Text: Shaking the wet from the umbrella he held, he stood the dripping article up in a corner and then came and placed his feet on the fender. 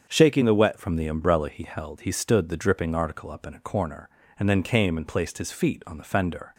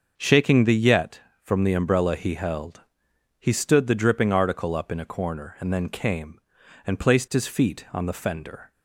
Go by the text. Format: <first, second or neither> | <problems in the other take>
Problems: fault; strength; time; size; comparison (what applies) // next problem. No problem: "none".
first | starts louder than the rest; noticeable; until 1.1 s; 6 dB; also in the first // says "yet" for "wet"; at 0.7 s